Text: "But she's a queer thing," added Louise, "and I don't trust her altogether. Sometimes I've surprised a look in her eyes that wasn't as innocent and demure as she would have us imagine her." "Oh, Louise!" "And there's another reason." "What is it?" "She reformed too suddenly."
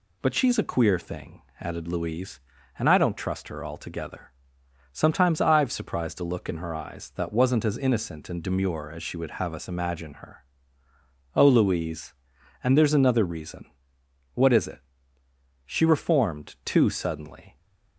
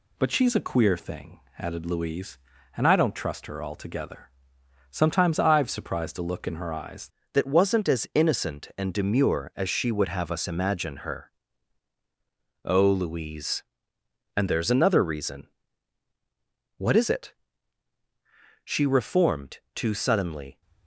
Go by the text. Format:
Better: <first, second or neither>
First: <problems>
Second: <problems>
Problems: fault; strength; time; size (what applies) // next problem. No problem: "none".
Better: first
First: none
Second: changes voice at "that"; from 7.3 s on; 13.3 s long